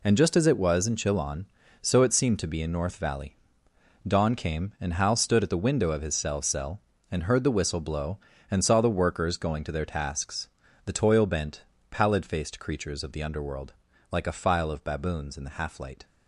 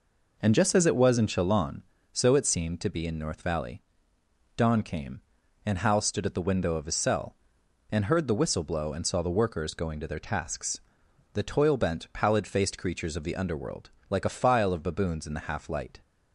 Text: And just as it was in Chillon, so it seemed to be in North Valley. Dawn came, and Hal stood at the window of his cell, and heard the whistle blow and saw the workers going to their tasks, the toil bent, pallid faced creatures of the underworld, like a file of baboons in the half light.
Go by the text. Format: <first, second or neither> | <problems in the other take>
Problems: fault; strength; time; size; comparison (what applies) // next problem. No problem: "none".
second | says "cell" twice; at 6.4 s